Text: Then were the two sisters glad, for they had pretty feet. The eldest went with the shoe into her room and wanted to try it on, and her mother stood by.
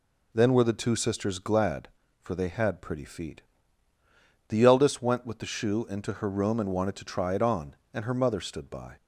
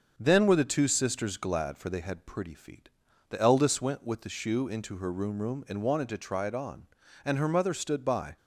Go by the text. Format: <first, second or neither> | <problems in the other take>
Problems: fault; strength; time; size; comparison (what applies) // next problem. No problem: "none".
first | starts louder than the rest; until 1.1 s; 6.5 dB // says "room" twice; at 5.4 s